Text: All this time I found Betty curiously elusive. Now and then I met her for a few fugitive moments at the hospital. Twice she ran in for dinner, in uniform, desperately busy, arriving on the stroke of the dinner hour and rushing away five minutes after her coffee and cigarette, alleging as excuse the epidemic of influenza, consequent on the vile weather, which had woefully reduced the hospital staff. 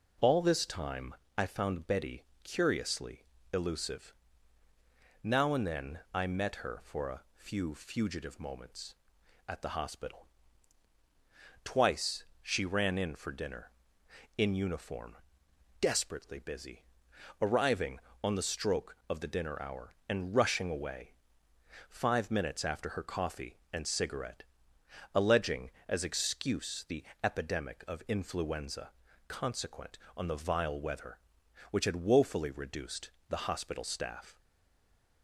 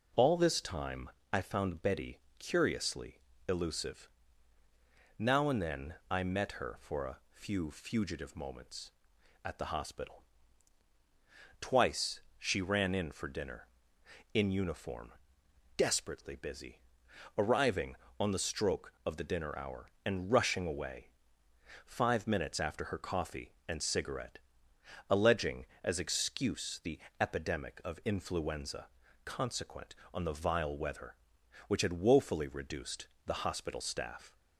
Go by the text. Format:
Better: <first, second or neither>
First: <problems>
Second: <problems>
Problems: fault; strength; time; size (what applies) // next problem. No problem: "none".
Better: second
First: pauses between "time" and "I"; slight; at 1.1 s; 0.22 s long // pauses between "Betty" and "curiously"; slight; at 2.2 s; 0.18 s long // pauses between "curiously" and "elusive"; slight; at 3.2 s; 0.30 s long // pauses between "Twice" and "she"; slight; at 12.2 s; 0.18 s long // pauses between "away" and "five"; noticeable; at 21.1 s; 0.76 s long // pauses between "the" and "epidemic"; slight; at 27.0 s; 0.18 s long // pauses between "reduced" and "the"; slight; at 33.1 s; 0.18 s long // stays silent after the last word; slight; from 34.3 s on; 0.9 s long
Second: pauses between "time" and "I"; slight; at 1.1 s; 0.22 s long // pauses between "Betty" and "curiously"; slight; at 2.2 s; 0.18 s long // pauses between "curiously" and "elusive"; slight; at 3.1 s; 0.30 s long // pauses between "Twice" and "she"; slight; at 12.2 s; 0.18 s long // pauses between "away" and "five"; noticeable; at 21.0 s; 0.76 s long // pauses between "the" and "epidemic"; slight; at 26.9 s; 0.20 s long // pauses between "reduced" and "the"; slight; at 33.0 s; 0.18 s long